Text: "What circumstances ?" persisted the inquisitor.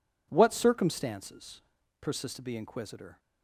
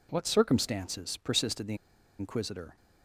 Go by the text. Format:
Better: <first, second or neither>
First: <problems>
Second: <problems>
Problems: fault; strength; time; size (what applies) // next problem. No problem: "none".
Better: first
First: none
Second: pauses between "the" and "inquisitor"; at 1.7 s; 0.43 s long